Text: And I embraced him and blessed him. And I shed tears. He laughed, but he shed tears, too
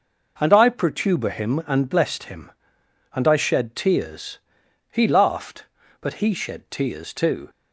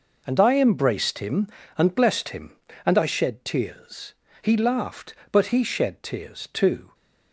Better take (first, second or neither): second